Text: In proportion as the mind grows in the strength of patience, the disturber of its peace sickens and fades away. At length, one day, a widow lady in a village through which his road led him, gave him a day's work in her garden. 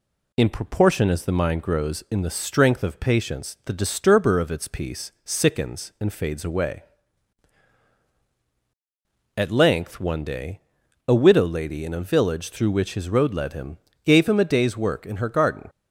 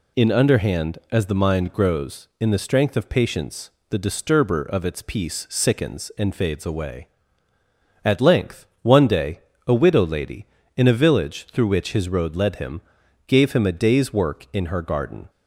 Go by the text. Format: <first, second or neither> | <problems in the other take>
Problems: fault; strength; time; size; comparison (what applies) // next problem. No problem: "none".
first | says "underhand" for "proportion"; at 0.2 s